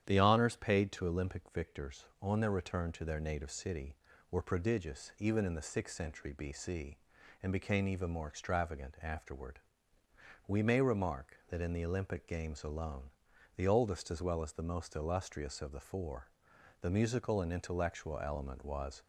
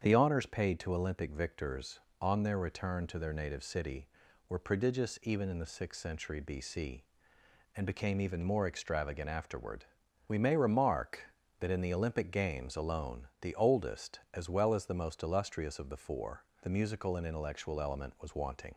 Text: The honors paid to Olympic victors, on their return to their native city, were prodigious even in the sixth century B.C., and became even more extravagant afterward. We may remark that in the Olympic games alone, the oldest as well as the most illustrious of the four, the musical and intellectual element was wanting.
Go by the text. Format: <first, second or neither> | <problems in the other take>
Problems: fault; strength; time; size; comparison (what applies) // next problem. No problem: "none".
second | starts louder than the rest; strong; until 1.0 s; 10 dB; strong in the second // stops before "wanting"; at 19.0 s